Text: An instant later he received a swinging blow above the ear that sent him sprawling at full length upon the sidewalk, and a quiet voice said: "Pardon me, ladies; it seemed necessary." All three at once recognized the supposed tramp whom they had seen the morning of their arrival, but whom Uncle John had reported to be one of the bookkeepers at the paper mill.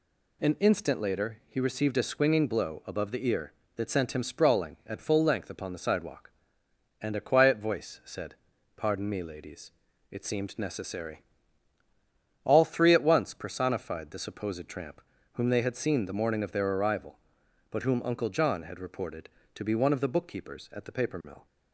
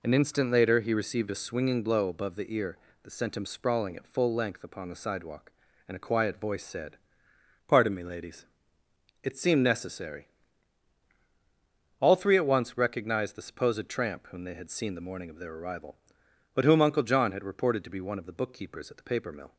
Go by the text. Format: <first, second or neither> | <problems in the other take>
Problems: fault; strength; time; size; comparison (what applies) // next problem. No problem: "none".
second | says "personified" for "recognized"; at 13.3 s // pauses between "tramp" and "whom"; slight; at 15.0 s; 0.32 s long